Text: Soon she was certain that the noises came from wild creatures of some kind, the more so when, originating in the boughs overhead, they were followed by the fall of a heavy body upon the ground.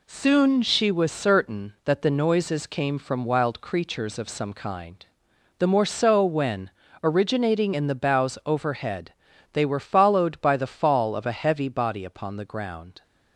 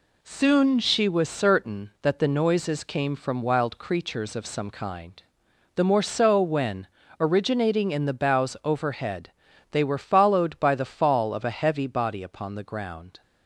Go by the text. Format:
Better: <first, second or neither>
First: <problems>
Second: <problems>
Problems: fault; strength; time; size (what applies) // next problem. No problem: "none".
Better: neither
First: none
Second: none